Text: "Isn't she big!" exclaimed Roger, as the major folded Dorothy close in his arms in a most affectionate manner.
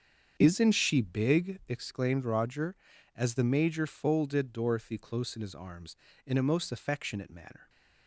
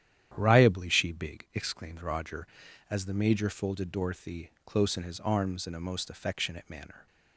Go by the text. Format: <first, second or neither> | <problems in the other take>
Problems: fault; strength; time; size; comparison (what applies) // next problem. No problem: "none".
first | starts louder than the rest; strong; until 1.3 s; 10 dB; strong in the first // says "Riably" for "Isn't"; at 0.3 s